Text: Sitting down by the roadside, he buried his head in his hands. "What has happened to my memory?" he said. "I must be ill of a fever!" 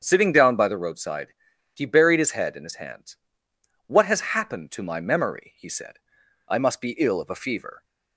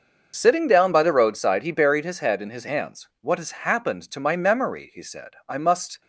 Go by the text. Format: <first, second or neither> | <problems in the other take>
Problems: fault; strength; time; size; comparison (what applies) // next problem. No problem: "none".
first | starts louder than the rest; noticeable; until 1.3 s; 6 dB; strong in the first // stops before "be ill of a fever"; at 6.0 s